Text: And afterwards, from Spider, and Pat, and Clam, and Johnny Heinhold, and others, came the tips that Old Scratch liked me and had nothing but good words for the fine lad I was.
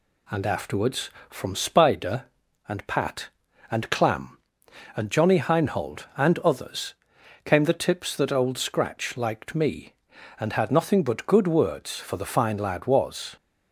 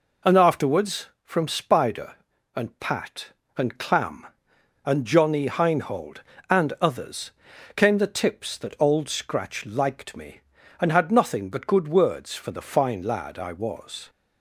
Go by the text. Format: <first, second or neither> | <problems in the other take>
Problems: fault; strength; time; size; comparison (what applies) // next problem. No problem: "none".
second | skips "I"; at 12.8 s